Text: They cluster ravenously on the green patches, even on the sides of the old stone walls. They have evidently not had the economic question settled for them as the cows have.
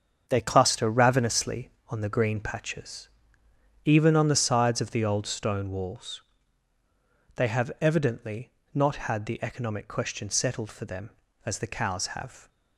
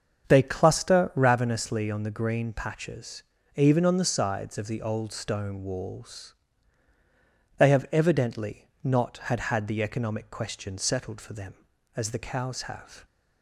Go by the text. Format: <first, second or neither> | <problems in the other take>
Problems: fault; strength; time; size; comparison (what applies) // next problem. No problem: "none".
first | starts louder than the rest; until 1.3 s; 7 dB; strong in the first // pauses between "evidently" and "not"; slight; at 8.6 s; 0.16 s long; slight in the first // says "had" twice; at 9.3 s